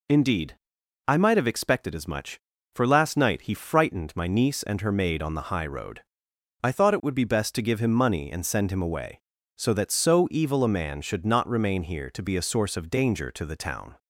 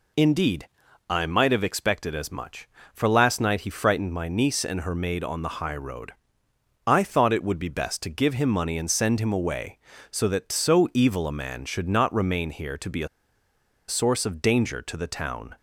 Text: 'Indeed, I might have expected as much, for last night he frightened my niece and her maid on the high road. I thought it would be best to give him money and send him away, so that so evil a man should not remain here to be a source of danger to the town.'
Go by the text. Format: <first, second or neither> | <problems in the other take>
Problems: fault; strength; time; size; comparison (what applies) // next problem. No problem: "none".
first | pauses between "a" and "source"; noticeable; at 13.0 s; 0.80 s long